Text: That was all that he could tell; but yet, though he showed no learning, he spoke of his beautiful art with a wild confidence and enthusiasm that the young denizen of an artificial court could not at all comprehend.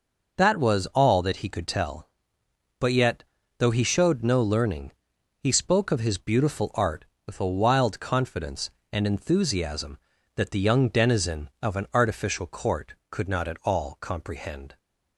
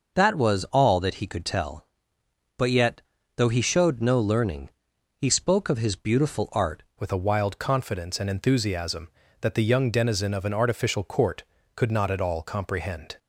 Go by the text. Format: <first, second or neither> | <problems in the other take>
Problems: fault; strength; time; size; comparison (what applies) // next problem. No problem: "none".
first | changes voice at "with"; from 7.0 s on; 6.1 s long